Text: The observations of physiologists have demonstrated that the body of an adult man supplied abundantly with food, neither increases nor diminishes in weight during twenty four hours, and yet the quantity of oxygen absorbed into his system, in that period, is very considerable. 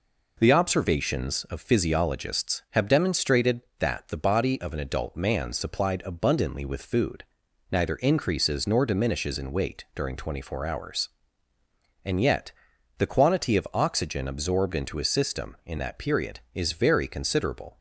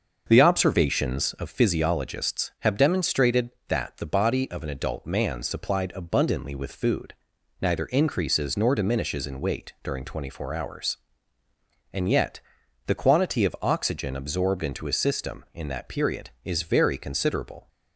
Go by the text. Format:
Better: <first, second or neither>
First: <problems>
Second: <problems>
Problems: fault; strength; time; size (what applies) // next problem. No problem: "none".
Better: first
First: pauses between "yet" and "the"; noticeable; at 12.5 s; 0.48 s long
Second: starts louder than the rest; until 1.7 s; 6.5 dB // pauses between "yet" and "the"; noticeable; at 12.3 s; 0.48 s long